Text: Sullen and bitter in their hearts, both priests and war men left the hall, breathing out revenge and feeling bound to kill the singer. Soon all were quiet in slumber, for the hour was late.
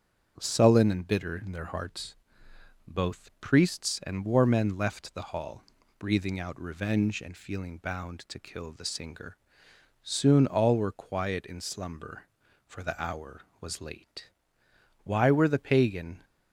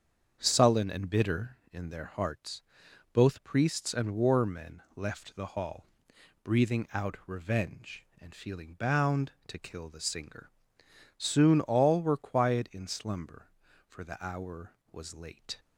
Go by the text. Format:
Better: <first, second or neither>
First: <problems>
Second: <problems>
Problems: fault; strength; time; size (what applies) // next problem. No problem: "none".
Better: second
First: starts louder than the rest; until 1.3 s; 6.5 dB // goes on to say "Why were the pagan"; noticeable; from 15.0 s on; 1.2 s long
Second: starts louder than the rest; strong; until 1.4 s; 7 dB